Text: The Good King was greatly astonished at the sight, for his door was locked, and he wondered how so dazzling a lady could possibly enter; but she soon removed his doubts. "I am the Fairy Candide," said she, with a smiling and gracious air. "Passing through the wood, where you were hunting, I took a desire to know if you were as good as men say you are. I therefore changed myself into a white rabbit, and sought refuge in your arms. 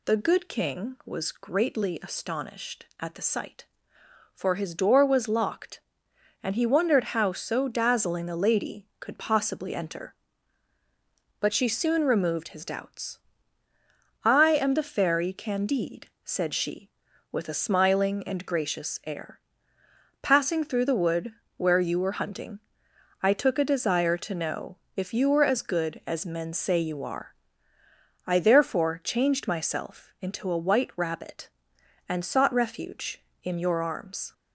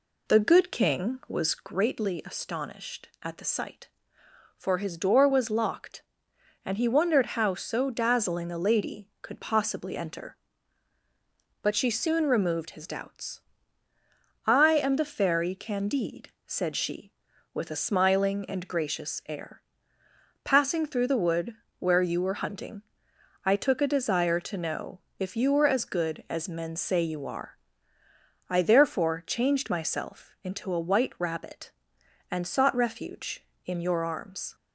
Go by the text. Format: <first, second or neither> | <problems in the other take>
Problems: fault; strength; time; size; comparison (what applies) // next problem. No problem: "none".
first | starts louder than the rest; slight; until 1.9 s; 2 dB // pauses between "know" and "if"; slight; at 24.9 s; 0.18 s long; slight in the first